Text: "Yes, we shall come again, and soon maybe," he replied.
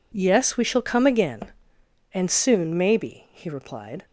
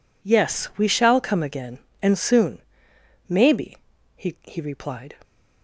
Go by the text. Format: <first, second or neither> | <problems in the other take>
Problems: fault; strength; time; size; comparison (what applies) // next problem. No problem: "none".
first | pauses between "soon" and "maybe"; noticeable; at 2.5 s; 0.70 s long // says "he" twice; at 4.4 s